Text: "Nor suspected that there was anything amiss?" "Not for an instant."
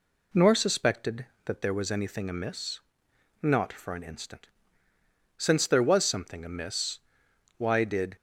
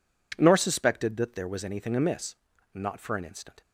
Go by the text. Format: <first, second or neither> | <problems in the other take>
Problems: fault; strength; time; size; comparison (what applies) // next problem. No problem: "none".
second | goes on to say "Since there was something amiss why did"; strong; from 5.3 s on; 2.8 s long